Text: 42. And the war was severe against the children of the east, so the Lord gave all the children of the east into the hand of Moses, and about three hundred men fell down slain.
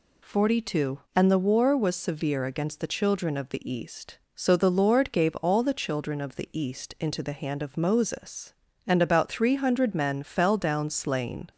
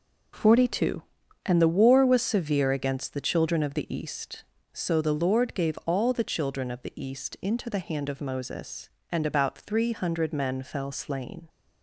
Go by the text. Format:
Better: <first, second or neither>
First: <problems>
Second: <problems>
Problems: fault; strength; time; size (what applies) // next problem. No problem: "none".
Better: first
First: none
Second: skips "down"; at 10.9 s